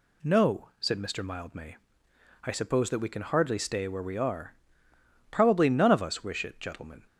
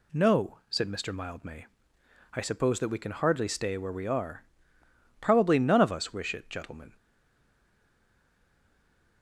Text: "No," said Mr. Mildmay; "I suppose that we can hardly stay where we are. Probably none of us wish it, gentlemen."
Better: first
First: none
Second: stays silent after the last word; from 6.9 s on; 2.3 s long

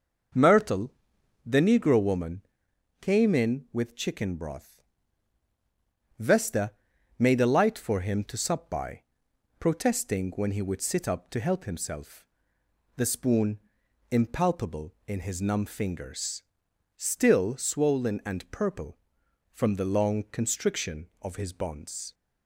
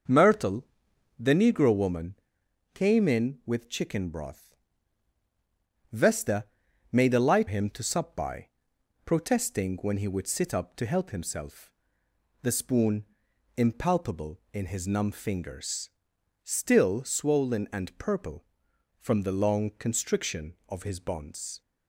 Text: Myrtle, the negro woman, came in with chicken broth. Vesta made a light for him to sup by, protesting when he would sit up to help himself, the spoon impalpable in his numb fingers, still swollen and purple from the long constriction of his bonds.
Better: first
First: pauses between "Vesta" and "made"; noticeable; at 6.7 s; 0.48 s long // pauses between "spoon" and "impalpable"; noticeable; at 13.5 s; 0.50 s long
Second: starts louder than the rest; until 1.6 s; 6 dB // pauses between "Vesta" and "made"; noticeable; at 6.4 s; 0.48 s long // skips "for"; at 7.4 s // pauses between "spoon" and "impalpable"; noticeable; at 13.0 s; 0.50 s long

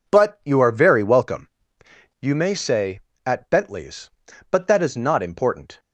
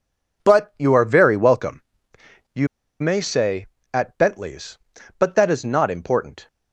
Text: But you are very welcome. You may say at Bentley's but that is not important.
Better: first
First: none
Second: pauses between "You" and "may"; slight; at 2.6 s; 0.35 s long

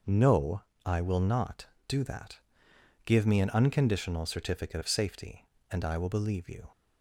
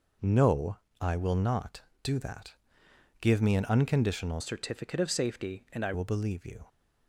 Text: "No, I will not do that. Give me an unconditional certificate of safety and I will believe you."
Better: first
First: none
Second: changes voice from "certificate" to "I"; from 4.4 to 5.9 s; 1.5 s long

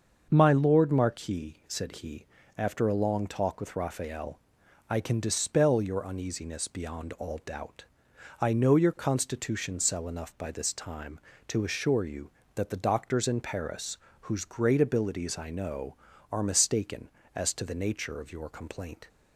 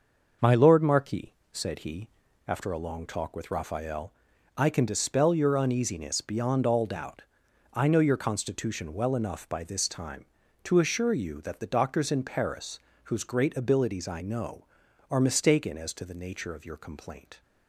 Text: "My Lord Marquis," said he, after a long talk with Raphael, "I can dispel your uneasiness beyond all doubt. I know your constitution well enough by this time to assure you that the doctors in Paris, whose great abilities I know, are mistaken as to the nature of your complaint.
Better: second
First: starts louder than the rest; until 1.3 s; 6.5 dB // says "cell" for "well"; at 9.7 s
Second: starts louder than the rest; noticeable; until 1.6 s; 6 dB

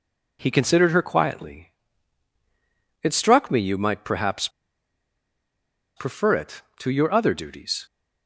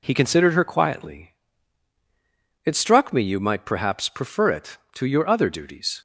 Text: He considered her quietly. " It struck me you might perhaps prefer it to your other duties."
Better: second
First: pauses between "perhaps" and "prefer"; strong; at 4.4 s; 1.4 s long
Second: none

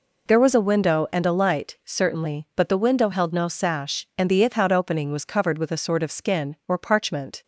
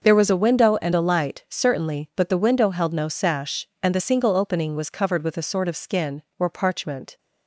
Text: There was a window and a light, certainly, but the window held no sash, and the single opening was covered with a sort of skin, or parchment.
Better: second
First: says "ithout" for "single"; at 4.4 s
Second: none

